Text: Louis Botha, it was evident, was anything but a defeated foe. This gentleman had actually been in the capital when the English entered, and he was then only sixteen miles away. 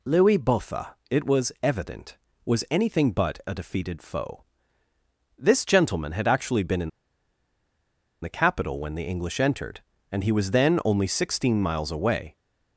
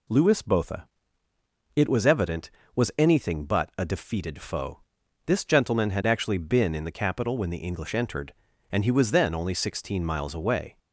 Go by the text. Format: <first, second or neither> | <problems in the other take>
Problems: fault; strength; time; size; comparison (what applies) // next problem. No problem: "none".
second | pauses between "in" and "the"; strong; at 6.8 s; 1.3 s long